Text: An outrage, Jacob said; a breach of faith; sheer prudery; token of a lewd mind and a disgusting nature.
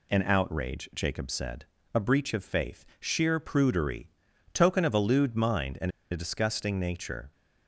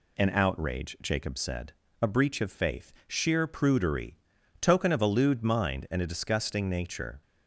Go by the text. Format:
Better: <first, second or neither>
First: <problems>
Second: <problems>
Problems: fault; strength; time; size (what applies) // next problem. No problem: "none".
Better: second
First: pauses between "and" and "a"; slight; at 5.9 s; 0.20 s long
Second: none